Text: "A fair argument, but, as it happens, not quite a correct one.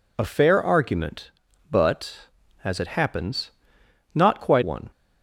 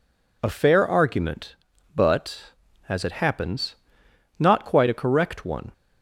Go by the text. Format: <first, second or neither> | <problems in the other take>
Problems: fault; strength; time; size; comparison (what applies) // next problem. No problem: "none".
second | skips "a correct"; at 4.6 s